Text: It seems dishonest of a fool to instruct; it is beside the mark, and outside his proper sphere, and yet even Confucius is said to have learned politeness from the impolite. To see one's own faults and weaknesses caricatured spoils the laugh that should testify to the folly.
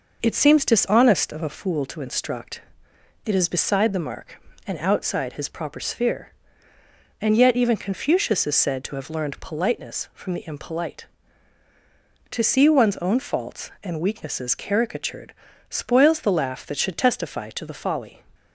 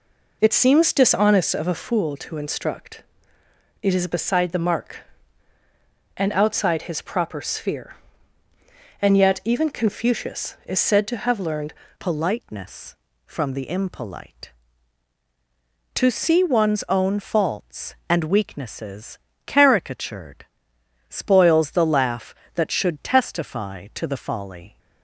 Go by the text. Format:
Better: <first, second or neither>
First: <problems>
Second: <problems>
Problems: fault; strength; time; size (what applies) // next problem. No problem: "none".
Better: first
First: pauses between "caricatured" and "spoils"; at 15.3 s; 0.38 s long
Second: changes voice at "politeness"; from 11.9 s on; 12.8 s long // pauses between "weaknesses" and "caricatured"; slight; at 19.1 s; 0.28 s long // pauses between "caricatured" and "spoils"; noticeable; at 20.4 s; 0.64 s long